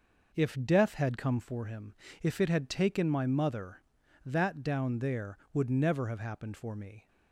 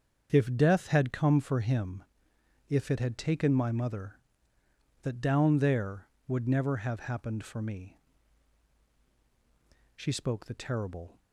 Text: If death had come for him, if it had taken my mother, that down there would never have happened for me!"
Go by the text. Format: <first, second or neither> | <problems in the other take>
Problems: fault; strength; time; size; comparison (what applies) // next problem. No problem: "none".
first | starts louder than the rest; until 1.3 s; 7 dB // goes on to say "She spoke the terrible"; noticeable; from 9.9 s on; 1.2 s long